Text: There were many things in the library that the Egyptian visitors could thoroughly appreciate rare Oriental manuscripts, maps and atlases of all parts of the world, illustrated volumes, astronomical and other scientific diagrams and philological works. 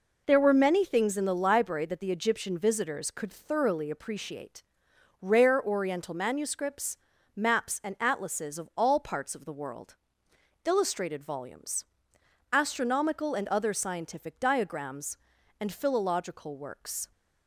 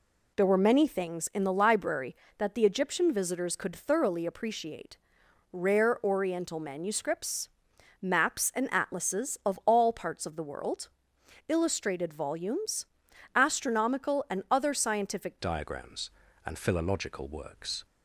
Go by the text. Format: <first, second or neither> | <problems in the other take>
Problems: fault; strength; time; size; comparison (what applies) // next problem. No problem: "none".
first | pauses between "appreciate" and "rare"; noticeable; at 4.9 s; 0.54 s long; noticeable in the first // changes voice at "diagrams"; from 15.3 s on; 2.5 s long